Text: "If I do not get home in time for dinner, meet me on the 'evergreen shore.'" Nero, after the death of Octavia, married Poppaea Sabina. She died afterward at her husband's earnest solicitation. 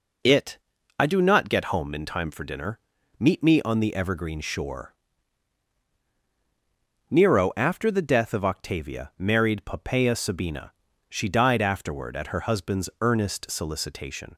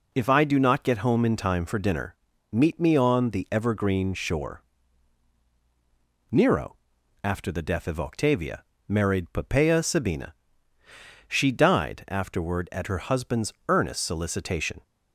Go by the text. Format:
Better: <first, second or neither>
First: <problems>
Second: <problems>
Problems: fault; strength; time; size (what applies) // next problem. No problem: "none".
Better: second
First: says "It" for "If"; at 0.2 s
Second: none